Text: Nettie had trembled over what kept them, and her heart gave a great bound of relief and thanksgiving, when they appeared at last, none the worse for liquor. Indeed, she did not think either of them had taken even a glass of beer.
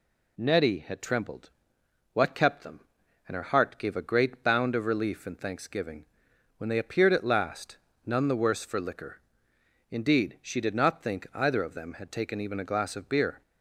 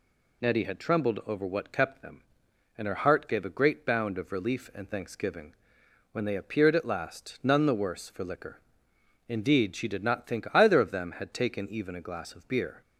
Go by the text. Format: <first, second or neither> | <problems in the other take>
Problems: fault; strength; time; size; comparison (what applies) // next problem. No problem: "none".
second | skips "over"; at 1.8 s